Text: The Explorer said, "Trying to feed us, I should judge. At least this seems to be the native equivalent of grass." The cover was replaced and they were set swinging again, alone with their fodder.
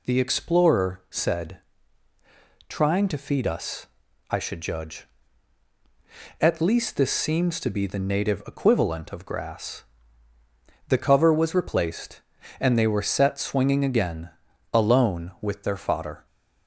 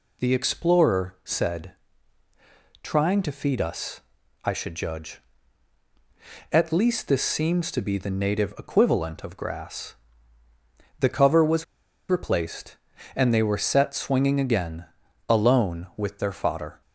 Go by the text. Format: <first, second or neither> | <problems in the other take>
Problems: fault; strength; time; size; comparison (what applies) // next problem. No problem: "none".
first | pauses between "was" and "replaced"; at 11.6 s; 0.44 s long